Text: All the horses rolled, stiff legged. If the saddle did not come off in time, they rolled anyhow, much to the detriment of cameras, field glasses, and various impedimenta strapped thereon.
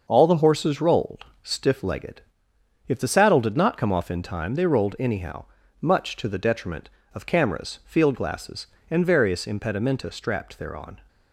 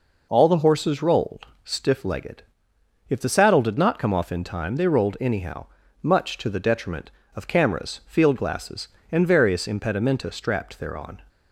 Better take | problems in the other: second | gets quieter; throughout; 6 dB

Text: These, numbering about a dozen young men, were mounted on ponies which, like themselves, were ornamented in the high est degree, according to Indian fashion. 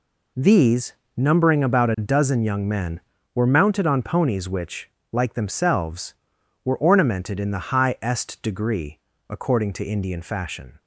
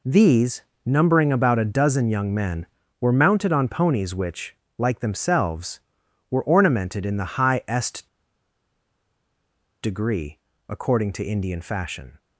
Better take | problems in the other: first | pauses between "est" and "degree"; strong; at 8.0 s; 1.7 s long

